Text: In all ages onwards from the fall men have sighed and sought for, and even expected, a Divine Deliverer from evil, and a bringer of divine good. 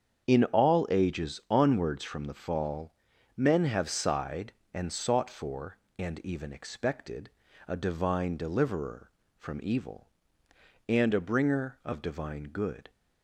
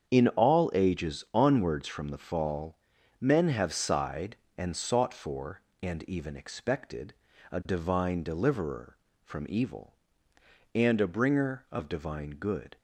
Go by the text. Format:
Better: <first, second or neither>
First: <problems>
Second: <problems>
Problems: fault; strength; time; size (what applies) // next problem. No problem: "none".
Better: neither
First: starts louder than the rest; strong; until 1.3 s; 7.5 dB // pauses between "fall" and "men"; at 2.9 s; 0.44 s long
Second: starts louder than the rest; strong; until 1.1 s; 7.5 dB // pauses between "fall" and "men"; at 2.7 s; 0.44 s long